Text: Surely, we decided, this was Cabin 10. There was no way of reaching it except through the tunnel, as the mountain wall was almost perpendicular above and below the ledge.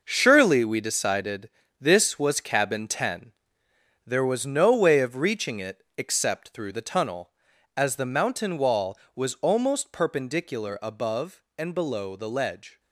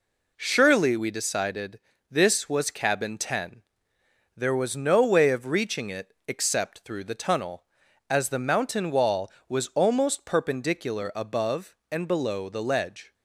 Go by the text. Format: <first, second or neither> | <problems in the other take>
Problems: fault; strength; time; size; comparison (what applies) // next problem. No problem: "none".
second | gets quieter; strong; throughout; 9.5 dB